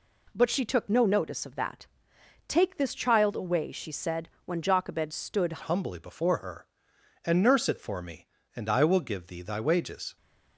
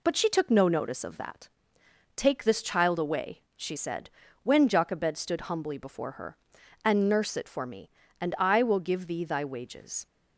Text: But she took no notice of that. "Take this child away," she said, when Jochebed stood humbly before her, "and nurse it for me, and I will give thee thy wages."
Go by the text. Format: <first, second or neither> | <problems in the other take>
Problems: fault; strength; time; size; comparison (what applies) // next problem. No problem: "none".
second | changes voice at "humbly"; from 5.6 s on; 4.5 s long